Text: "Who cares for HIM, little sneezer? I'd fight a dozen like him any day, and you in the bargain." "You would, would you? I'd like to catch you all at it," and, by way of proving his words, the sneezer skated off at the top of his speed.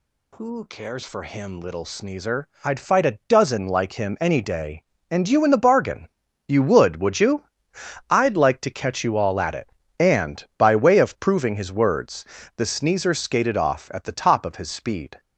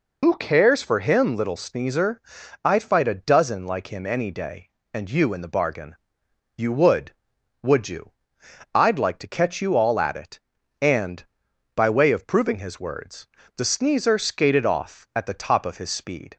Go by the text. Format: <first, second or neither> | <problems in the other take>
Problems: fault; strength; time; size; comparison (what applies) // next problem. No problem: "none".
first | loses the start of "Who"; at 0.2 s; 85 ms